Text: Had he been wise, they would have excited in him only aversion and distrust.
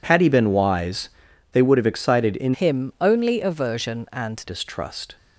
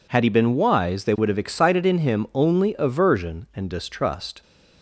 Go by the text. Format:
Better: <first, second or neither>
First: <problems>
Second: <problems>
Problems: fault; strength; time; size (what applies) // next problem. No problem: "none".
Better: second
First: changes voice from "him" to "and"; from 2.5 to 4.4 s; 1.9 s long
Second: none